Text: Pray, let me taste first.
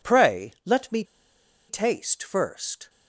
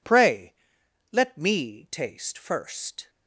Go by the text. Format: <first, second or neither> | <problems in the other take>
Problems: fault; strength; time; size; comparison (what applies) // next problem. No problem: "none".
second | pauses between "me" and "taste"; noticeable; at 1.0 s; 0.63 s long